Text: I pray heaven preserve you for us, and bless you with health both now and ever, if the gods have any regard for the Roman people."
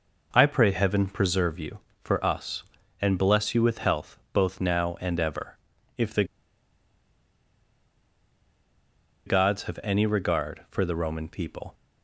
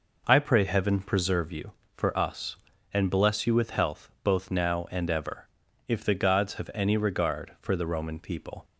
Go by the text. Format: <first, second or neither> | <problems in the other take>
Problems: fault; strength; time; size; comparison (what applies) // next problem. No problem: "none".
second | pauses between "the" and "gods"; strong; at 6.2 s; 3.0 s long